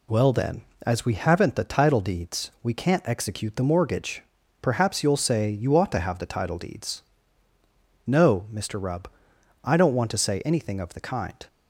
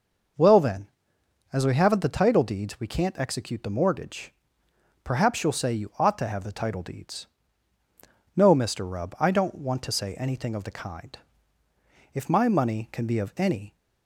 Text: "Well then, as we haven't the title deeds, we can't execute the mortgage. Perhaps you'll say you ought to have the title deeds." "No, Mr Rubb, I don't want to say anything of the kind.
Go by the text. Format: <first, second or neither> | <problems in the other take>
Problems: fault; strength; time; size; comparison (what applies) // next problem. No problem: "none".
first | goes on to say "If my money can be of any"; from 12.1 s on; 1.6 s long